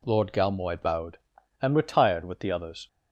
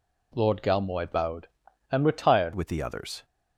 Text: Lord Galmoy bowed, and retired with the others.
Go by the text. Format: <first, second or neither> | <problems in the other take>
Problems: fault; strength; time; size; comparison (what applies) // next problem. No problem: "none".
first | changes voice at "with"; from 2.5 s on; 0.7 s long